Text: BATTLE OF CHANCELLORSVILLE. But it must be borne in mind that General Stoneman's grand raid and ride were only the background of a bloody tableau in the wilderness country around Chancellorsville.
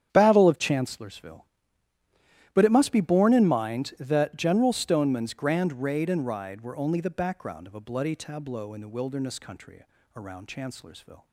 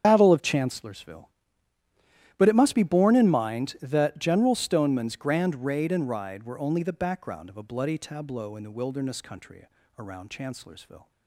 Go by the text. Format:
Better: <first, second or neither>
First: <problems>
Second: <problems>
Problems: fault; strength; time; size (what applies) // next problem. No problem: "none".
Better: first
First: starts louder than the rest; strong; until 1.1 s; 9.5 dB // pauses between "country" and "around"; slight; at 9.8 s; 0.34 s long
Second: loses the start of "BATTLE"; at 0.0 s; 90 ms // starts louder than the rest; strong; until 1.0 s; 8 dB // pauses between "country" and "around"; slight; at 9.6 s; 0.34 s long